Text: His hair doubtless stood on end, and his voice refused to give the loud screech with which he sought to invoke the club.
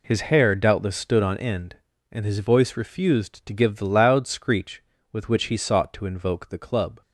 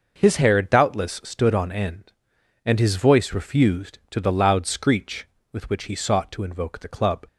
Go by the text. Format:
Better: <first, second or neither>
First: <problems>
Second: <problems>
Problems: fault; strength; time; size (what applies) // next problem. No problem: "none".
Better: first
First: none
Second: skips "give"; at 4.2 s